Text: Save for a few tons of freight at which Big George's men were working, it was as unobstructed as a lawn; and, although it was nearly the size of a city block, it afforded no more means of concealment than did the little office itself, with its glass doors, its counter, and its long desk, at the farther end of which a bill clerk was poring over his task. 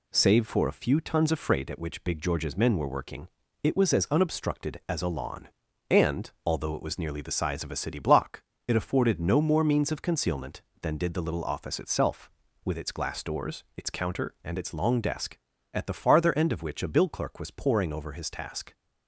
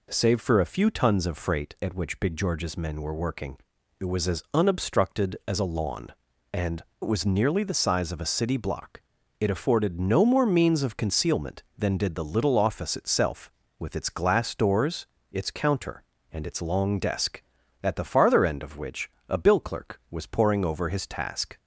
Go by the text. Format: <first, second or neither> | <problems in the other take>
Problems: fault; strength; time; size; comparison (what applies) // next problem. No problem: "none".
first | skips "although"; at 6.9 s // pauses between "which" and "a"; slight; at 19.0 s; 0.20 s long